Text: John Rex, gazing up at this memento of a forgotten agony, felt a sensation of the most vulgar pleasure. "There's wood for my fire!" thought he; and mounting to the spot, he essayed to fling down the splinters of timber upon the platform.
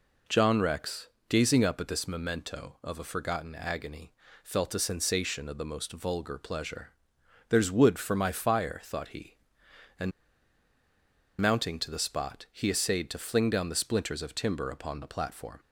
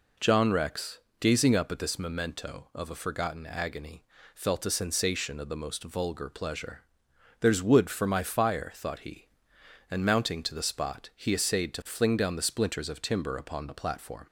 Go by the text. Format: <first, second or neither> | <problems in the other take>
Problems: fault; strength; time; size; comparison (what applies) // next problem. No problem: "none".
second | pauses between "and" and "mounting"; strong; at 10.1 s; 1.2 s long